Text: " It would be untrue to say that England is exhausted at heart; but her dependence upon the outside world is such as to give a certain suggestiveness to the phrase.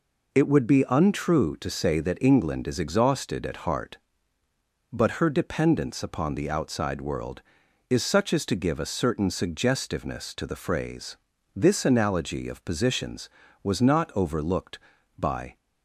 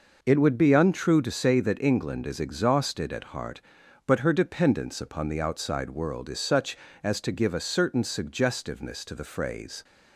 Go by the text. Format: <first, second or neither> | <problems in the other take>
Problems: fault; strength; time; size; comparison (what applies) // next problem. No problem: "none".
second | goes on to say "This analogy of positions was not overlooked by"; strong; from 11.5 s on; 4.0 s long